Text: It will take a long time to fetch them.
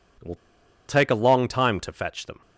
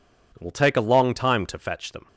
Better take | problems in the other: second | pauses between "will" and "take"; noticeable; at 0.3 s; 0.52 s long

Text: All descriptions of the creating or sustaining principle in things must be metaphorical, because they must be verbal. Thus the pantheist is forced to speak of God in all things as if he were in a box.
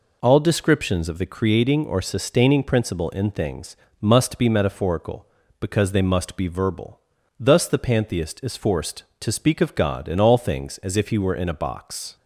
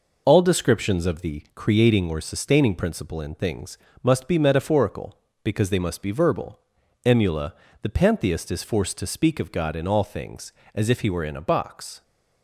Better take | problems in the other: first | pauses between "things" and "must"; slight; at 3.7 s; 0.24 s long; slight in the first // says "Emula" for "Thus"; at 7.0 s

